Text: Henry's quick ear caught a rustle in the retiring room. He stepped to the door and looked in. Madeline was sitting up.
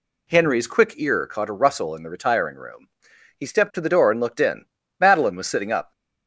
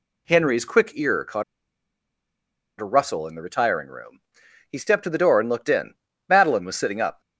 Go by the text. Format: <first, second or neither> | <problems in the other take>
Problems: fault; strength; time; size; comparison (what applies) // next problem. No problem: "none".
first | pauses between "caught" and "a"; strong; at 1.4 s; 1.3 s long